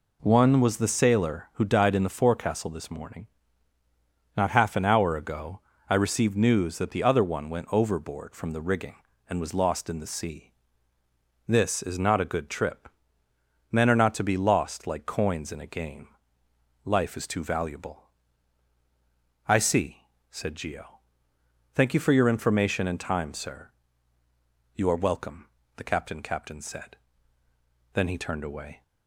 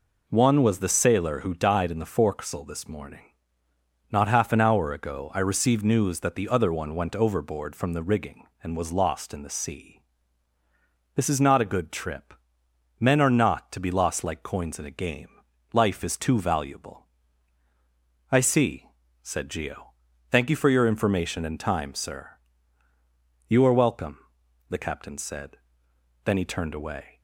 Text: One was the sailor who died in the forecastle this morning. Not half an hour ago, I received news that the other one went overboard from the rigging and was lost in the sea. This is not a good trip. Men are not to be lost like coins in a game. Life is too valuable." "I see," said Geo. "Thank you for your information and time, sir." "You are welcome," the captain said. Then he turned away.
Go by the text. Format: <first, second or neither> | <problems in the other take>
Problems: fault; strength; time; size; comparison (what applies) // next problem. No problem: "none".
second | says "captain" twice; at 26.2 s